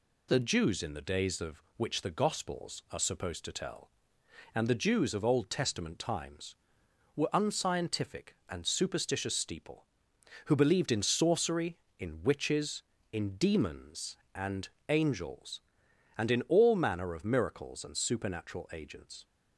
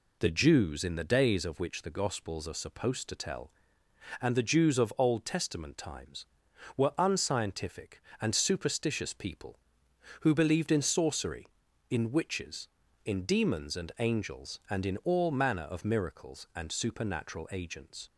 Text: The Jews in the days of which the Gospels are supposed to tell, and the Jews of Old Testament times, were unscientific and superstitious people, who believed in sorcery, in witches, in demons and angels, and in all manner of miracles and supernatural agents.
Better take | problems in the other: second | says "steeple" for "people"; at 9.3 s // pauses between "and" and "angels"; slight; at 14.6 s; 0.22 s long

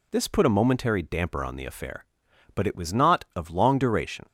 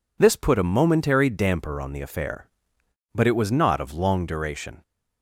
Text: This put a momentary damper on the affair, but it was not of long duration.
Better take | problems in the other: neither | none

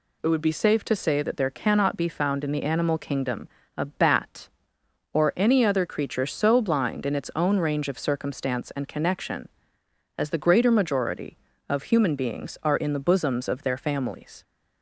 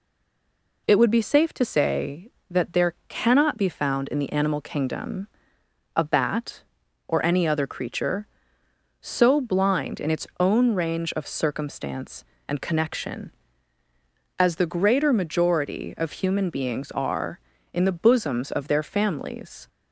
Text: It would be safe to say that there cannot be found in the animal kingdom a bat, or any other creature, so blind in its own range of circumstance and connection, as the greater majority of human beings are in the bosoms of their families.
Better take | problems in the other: first | stays silent before the first word; slight; until 0.8 s; 0.8 s long // pauses between "kingdom" and "a"; noticeable; at 5.2 s; 0.68 s long; slight in the first

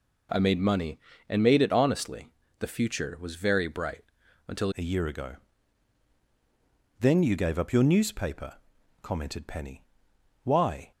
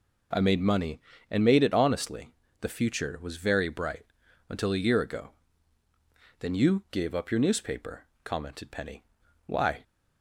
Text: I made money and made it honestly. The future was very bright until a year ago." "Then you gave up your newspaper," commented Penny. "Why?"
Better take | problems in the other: second | pauses between "bright" and "until"; at 4.0 s; 0.42 s long; also in the second // changes voice at "a"; from 4.7 s on; 6.2 s long

